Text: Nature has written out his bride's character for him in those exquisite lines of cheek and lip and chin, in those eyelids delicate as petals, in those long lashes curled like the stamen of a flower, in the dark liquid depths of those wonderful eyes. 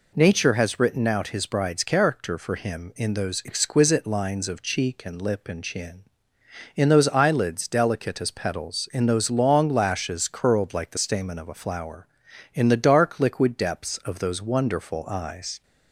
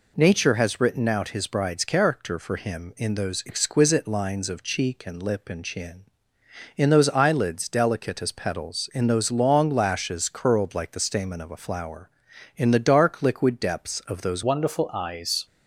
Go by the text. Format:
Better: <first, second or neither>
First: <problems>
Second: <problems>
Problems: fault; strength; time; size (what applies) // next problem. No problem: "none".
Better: first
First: none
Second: changes voice at "wonderful"; from 14.4 s on; 1.0 s long